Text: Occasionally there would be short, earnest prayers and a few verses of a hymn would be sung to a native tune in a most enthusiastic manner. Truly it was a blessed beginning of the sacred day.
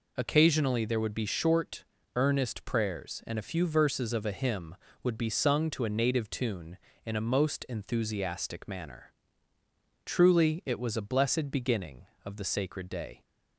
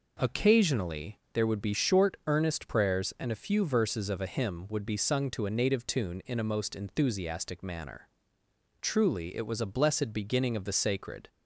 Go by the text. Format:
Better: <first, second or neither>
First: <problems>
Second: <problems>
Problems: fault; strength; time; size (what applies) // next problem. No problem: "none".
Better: first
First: none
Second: stops before "day"; at 11.2 s